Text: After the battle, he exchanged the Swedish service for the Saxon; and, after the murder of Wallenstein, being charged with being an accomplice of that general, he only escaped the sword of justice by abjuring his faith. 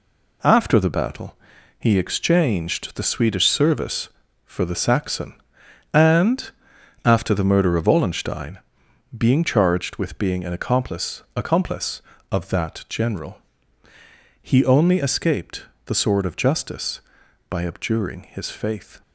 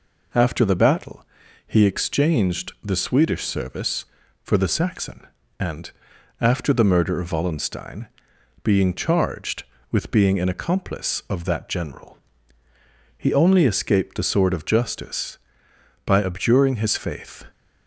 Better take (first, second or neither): second